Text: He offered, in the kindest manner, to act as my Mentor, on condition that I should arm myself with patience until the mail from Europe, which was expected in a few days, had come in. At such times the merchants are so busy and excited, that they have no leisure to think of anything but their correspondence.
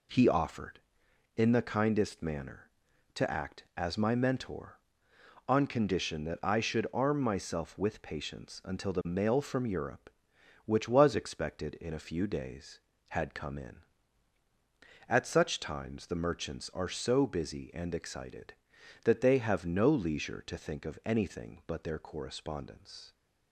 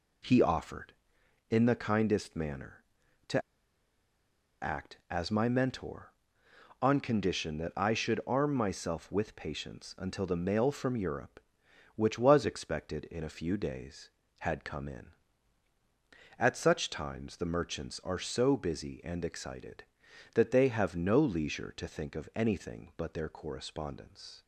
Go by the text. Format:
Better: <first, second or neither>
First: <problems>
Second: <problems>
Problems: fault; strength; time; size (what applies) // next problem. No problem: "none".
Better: first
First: none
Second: pauses between "to" and "act"; at 3.4 s; 1.2 s long